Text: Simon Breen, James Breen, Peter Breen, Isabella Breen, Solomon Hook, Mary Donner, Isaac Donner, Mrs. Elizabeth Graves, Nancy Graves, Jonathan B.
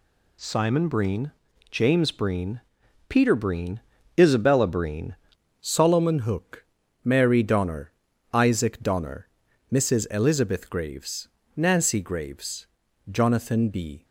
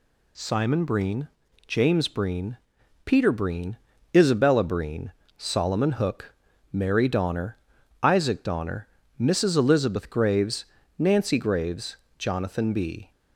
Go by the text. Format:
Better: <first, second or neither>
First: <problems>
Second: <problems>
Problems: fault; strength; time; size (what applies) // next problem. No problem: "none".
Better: second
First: changes voice at "Solomon"; from 5.6 s on; 8.4 s long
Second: none